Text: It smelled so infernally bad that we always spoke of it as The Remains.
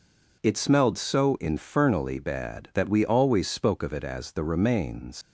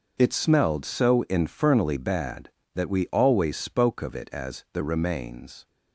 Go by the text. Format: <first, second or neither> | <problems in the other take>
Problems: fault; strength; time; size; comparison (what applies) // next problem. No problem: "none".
second | leaves "Remains" unfinished; at 5.2 s; 110 ms